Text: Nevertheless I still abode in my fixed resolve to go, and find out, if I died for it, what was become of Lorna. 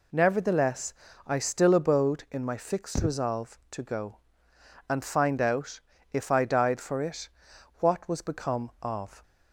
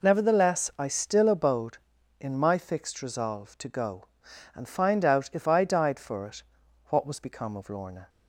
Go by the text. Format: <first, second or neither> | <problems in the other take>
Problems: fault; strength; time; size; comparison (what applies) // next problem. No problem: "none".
second | pauses between "Nevertheless" and "I"; slight; at 0.9 s; 0.32 s long // stops before "Lorna"; at 9.2 s